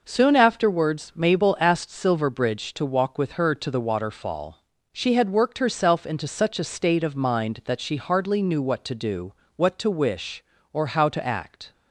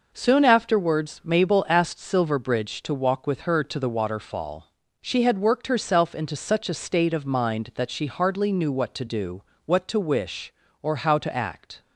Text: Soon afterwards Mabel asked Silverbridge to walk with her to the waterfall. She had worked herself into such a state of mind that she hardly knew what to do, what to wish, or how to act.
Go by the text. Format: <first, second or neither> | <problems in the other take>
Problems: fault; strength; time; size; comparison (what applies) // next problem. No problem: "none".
neither | none